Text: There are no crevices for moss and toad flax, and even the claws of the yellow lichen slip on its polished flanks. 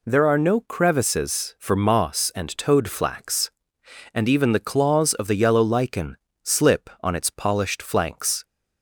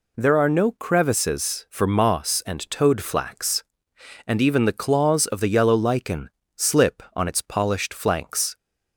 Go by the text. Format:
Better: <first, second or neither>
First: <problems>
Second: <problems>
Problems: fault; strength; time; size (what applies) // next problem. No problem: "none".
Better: neither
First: pauses between "lichen" and "slip"; slight; at 6.1 s; 0.24 s long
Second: pauses between "lichen" and "slip"; slight; at 6.3 s; 0.24 s long